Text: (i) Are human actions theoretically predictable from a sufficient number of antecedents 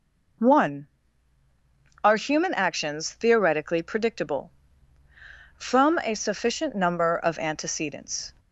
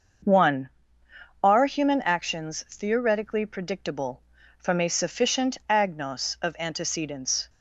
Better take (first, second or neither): first